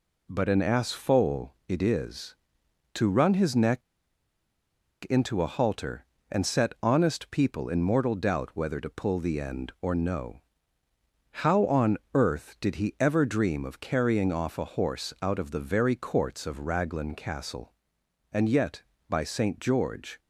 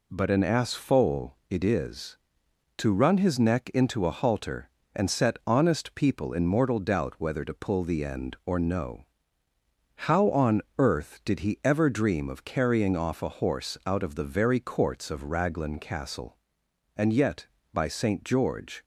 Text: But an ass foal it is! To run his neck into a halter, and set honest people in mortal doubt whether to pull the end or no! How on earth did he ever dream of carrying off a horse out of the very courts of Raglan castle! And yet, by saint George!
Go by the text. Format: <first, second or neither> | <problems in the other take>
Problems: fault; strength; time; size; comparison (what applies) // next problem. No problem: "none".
second | pauses between "neck" and "into"; strong; at 3.8 s; 1.2 s long